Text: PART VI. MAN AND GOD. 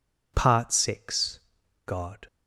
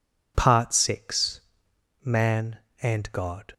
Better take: second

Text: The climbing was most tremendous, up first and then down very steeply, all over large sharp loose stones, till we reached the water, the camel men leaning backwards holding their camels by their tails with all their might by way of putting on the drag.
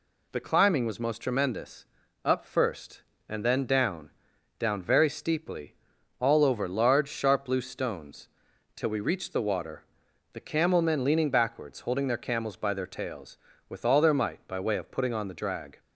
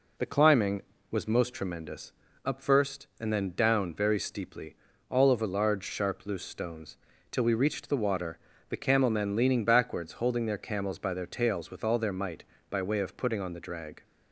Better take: second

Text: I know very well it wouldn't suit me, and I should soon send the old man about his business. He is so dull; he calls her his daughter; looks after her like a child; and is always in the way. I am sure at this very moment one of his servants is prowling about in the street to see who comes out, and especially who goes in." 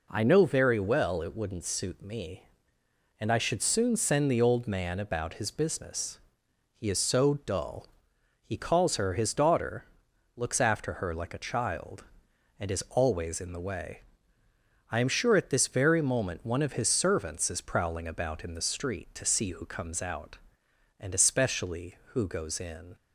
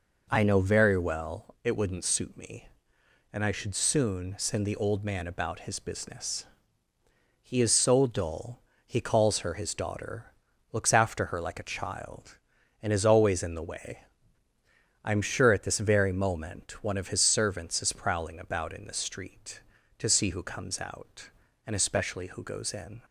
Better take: neither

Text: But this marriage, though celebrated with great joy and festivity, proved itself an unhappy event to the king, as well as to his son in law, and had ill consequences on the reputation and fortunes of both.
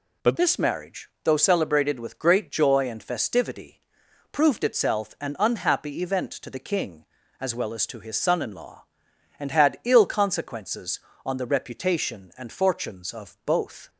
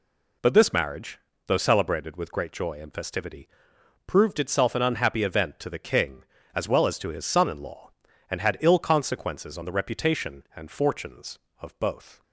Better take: second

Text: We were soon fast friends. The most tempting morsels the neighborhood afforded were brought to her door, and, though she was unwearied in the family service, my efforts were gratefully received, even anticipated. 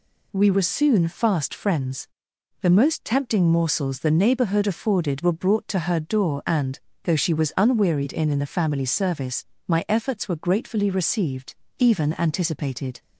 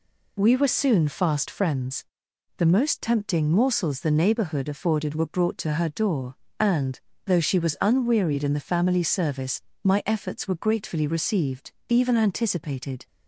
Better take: second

